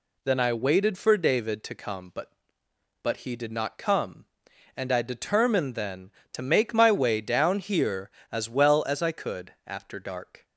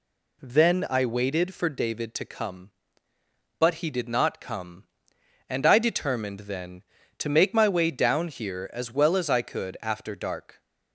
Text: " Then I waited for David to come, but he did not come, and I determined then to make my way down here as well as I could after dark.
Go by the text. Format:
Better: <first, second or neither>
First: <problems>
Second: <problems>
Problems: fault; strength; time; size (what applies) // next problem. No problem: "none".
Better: second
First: says "but" twice; at 3.0 s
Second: none